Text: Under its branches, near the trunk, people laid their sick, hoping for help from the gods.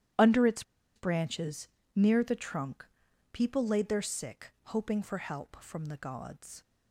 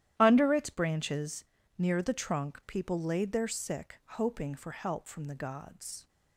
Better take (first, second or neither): second